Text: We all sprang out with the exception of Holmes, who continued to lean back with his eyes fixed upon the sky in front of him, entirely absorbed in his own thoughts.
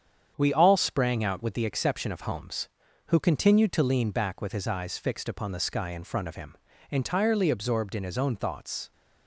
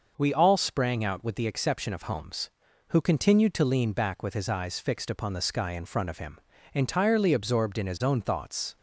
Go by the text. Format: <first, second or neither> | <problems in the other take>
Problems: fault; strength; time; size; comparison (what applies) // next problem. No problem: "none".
second | gets quieter; noticeable; throughout; 5.5 dB